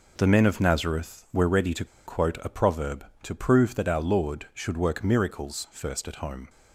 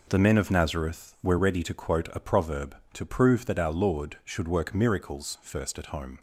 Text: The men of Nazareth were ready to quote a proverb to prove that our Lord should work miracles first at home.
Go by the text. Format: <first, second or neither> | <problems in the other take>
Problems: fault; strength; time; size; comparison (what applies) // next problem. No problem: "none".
second | pauses between "to" and "quote"; slight; at 1.8 s; 0.21 s long